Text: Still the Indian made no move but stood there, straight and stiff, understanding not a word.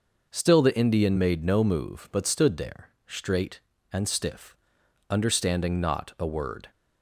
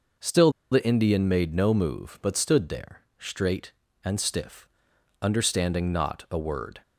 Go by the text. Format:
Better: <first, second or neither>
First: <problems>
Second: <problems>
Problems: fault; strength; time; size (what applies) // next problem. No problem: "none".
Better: first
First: none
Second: pauses between "Still" and "the"; slight; at 0.5 s; 0.21 s long